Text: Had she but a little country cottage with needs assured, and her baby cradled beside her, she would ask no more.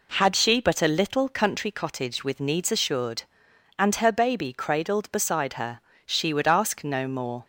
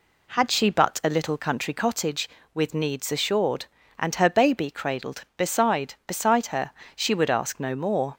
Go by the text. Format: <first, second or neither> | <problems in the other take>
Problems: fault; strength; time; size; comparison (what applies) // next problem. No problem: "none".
first | says "beside" twice; at 6.0 s